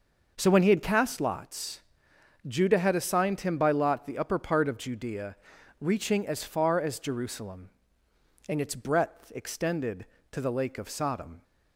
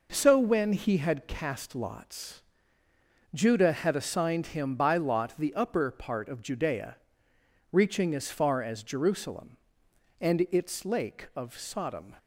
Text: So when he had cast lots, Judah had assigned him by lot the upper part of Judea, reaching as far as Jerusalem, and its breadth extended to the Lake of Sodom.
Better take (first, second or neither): first